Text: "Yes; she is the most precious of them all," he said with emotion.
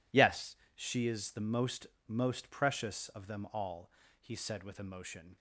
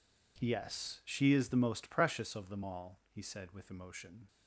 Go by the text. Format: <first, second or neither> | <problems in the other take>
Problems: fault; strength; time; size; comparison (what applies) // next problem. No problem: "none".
second | says "most" twice; at 2.0 s